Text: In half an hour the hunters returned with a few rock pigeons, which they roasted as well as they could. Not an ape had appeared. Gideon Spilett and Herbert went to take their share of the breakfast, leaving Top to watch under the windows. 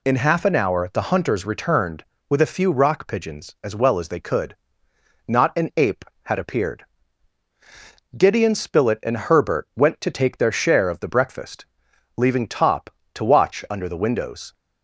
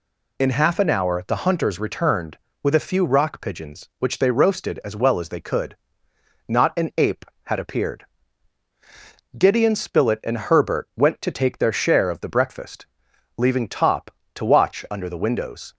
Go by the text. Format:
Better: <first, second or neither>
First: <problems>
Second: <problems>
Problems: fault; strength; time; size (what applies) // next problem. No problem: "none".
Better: second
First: skips "which they roasted"; at 3.5 s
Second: none